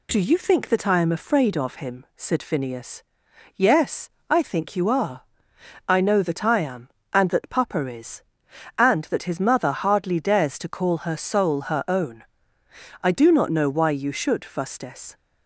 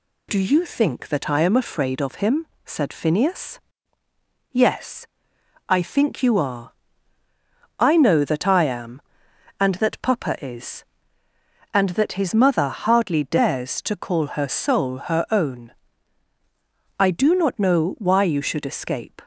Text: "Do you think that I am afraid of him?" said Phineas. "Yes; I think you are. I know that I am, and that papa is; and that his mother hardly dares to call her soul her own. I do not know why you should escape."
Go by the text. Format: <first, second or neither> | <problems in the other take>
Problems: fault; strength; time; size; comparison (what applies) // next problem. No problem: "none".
second | says "fustes" for "escape"; at 14.4 s